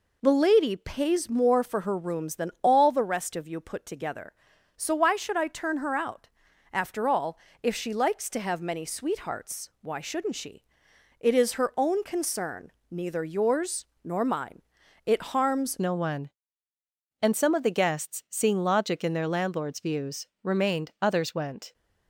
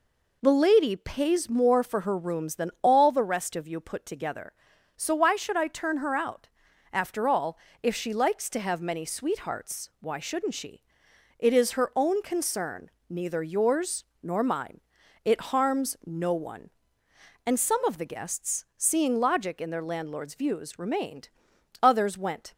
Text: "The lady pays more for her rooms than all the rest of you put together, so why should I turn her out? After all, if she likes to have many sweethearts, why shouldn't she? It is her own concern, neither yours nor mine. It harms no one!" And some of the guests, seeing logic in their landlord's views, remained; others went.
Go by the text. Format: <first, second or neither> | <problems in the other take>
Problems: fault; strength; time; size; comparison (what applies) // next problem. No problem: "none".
second | pauses between "yours" and "nor"; slight; at 13.8 s; 0.18 s long; slight in the second // changes voice at "no"; from 15.7 s on; 6.0 s long